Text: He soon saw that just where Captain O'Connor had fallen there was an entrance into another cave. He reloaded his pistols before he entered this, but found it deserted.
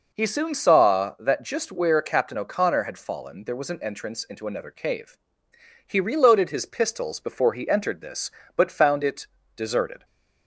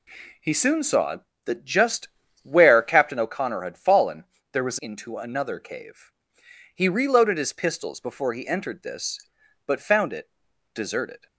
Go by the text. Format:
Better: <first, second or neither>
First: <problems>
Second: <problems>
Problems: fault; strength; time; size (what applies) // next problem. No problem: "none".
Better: first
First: pauses between "it" and "deserted"; slight; at 9.2 s; 0.28 s long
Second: pauses between "just" and "where"; slight; at 2.0 s; 0.36 s long // pauses between "fallen" and "there"; slight; at 4.2 s; 0.28 s long // skips "an entrance"; at 4.7 s // pauses between "it" and "deserted"; at 10.3 s; 0.42 s long